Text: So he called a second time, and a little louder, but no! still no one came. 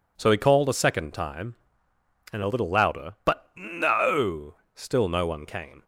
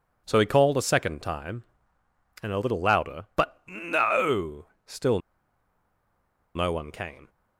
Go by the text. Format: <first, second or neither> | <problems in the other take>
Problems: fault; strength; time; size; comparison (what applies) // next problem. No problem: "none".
first | pauses between "still" and "no"; strong; at 5.1 s; 1.3 s long